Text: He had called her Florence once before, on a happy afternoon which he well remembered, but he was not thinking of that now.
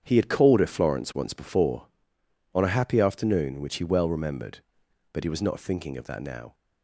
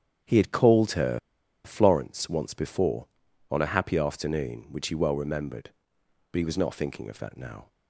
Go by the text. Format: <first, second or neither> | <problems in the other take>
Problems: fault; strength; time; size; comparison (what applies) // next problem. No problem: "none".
first | starts louder than the rest; strong; until 1.7 s; 8.5 dB; strong in the first // pauses between "her" and "Florence"; at 1.1 s; 0.45 s long